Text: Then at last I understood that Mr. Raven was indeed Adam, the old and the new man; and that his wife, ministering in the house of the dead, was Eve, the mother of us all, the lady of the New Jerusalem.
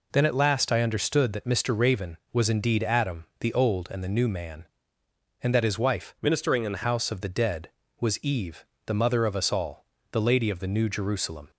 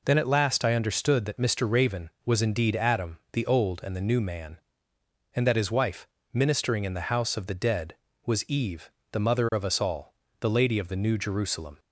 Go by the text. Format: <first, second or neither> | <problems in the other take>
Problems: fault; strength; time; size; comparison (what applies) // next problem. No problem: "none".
second | changes voice from "ministering" to "the"; from 6.2 to 6.8 s; 0.6 s long